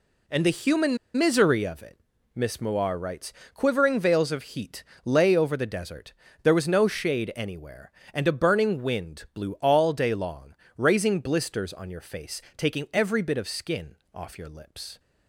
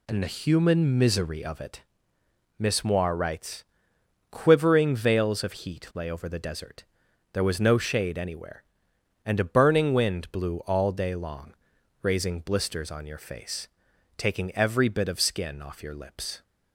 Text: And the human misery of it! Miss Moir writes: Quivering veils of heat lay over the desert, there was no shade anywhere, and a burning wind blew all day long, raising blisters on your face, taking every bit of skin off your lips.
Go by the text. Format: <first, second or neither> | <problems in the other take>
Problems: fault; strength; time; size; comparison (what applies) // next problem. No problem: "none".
second | pauses between "human" and "misery"; slight; at 0.9 s; 0.19 s long // pauses between "heat" and "lay"; slight; at 4.8 s; 0.22 s long // pauses between "skin" and "off"; slight; at 13.9 s; 0.18 s long